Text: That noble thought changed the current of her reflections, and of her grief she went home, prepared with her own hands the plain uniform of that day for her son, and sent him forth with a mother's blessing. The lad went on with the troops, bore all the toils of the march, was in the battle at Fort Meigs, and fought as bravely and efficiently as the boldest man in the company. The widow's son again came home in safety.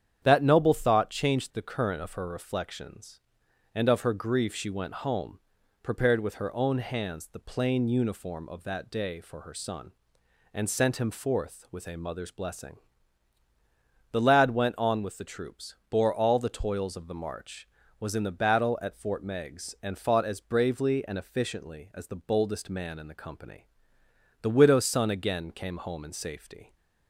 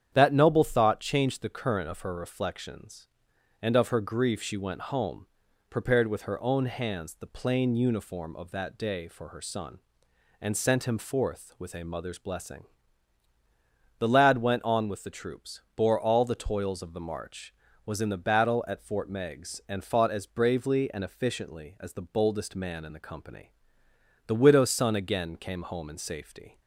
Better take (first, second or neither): neither